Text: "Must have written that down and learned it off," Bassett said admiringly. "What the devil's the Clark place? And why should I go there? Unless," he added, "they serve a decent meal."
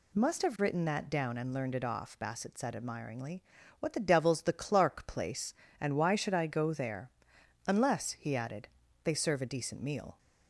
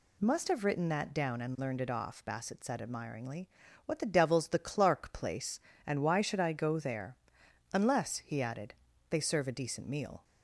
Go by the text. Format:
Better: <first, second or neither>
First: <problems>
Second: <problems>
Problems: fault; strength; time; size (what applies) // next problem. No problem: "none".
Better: neither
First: none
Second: none